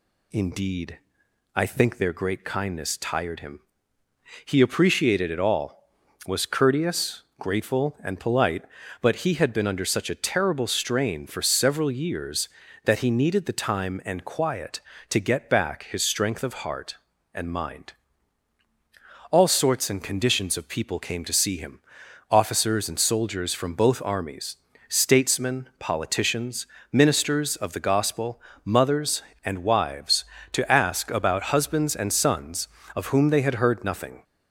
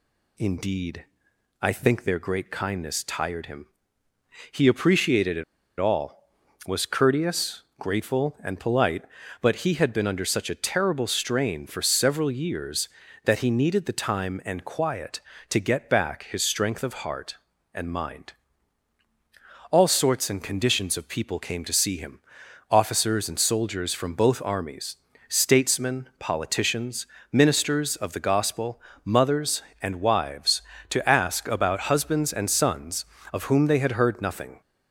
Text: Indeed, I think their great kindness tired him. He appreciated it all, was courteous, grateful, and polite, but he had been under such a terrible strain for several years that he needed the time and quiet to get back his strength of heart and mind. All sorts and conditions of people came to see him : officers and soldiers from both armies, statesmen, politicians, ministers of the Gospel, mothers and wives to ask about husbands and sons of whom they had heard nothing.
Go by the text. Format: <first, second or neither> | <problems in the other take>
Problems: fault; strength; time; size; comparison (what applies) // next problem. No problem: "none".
first | pauses between "it" and "all"; at 5.4 s; 0.36 s long